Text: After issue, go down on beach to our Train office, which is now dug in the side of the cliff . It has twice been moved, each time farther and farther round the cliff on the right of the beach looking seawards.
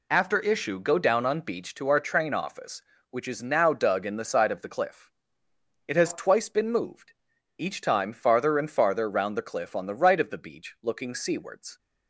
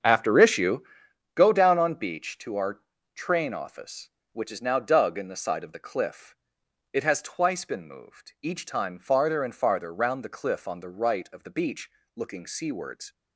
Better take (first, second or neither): first